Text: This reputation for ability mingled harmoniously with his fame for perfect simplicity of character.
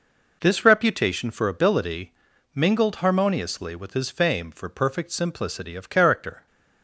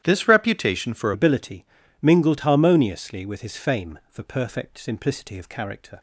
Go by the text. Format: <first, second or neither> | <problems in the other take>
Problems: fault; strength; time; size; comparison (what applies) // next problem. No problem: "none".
first | starts louder than the rest; strong; until 1.0 s; 11.5 dB // changes voice at "ability"; from 1.1 s on; 4.8 s long // pauses between "ability" and "mingled"; slight; at 1.6 s; 0.36 s long; also in the first